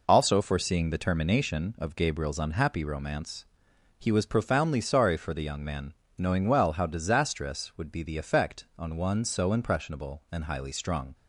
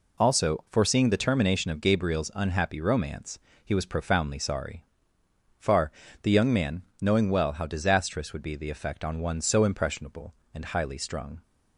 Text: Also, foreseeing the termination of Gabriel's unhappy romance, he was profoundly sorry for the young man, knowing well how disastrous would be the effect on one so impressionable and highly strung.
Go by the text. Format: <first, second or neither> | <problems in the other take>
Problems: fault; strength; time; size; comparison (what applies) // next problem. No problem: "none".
first | says "far" for "for"; at 5.5 s